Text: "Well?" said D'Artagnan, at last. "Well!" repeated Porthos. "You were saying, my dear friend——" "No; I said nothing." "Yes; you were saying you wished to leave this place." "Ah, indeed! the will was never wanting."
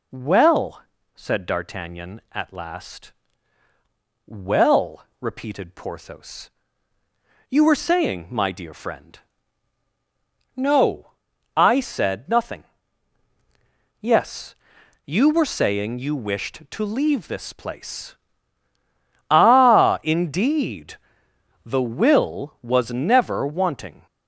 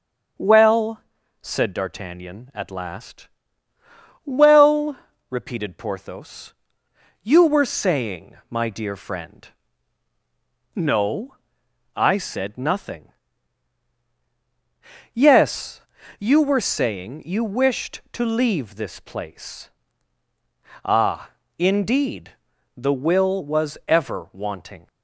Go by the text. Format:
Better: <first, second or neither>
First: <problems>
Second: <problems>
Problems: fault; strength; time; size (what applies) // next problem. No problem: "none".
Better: first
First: none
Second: starts louder than the rest; until 1.7 s; 6.5 dB // says "ever" for "never"; at 23.8 s